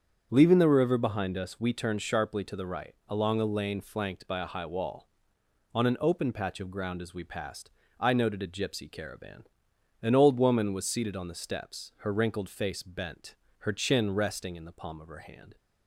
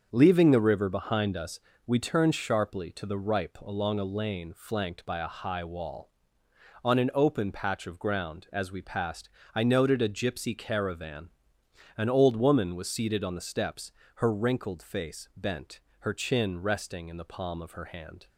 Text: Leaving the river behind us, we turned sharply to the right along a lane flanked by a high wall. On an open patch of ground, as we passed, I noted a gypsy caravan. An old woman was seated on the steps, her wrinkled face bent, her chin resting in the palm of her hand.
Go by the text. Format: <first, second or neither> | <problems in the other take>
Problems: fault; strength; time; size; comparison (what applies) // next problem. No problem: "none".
first | starts louder than the rest; until 1.1 s; 7 dB; strong in the first // says "ripe" for "right"; at 3.1 s